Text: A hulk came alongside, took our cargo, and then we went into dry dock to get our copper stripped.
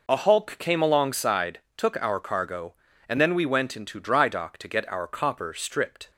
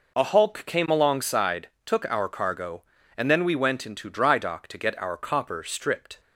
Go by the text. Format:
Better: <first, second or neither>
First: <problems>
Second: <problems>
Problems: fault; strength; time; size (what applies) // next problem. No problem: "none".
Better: neither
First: none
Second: none